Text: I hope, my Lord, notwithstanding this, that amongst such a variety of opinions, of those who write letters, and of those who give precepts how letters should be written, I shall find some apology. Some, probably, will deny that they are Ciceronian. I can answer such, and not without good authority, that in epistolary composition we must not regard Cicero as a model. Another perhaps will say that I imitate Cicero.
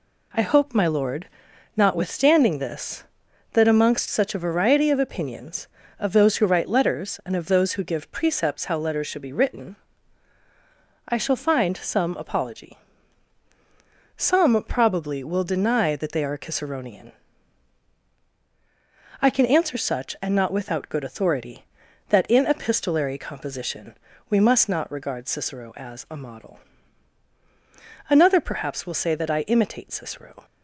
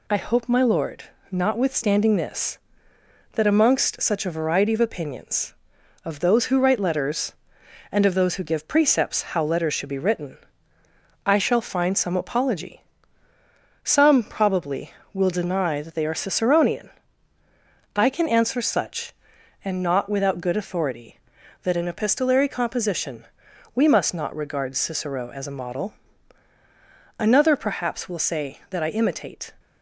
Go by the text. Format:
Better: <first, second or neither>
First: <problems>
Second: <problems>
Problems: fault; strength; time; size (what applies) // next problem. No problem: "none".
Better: first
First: pauses between "composition" and "we"; slight; at 23.9 s; 0.34 s long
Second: pauses between "composition" and "we"; noticeable; at 23.2 s; 0.50 s long // stops before "Cicero"; at 29.5 s